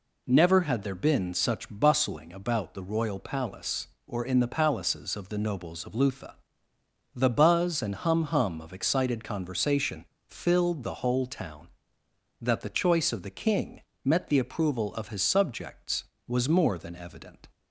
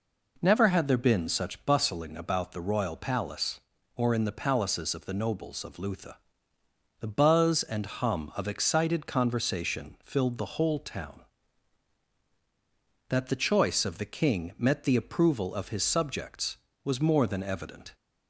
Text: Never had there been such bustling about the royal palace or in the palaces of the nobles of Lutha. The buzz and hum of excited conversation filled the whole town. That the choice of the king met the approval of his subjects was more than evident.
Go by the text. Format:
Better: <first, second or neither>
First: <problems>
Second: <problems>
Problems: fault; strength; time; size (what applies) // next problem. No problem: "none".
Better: second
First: says "hum" twice; at 8.2 s // pauses between "conversation" and "filled"; slight; at 10.0 s; 0.24 s long // pauses between "king" and "met"; slight; at 13.8 s; 0.22 s long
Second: none